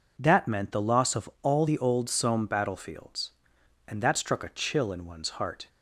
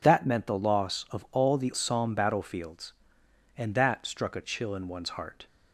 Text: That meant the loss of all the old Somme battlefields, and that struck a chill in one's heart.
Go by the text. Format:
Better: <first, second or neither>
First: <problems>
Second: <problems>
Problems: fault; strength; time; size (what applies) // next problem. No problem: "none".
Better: first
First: none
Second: skips "old"; at 1.7 s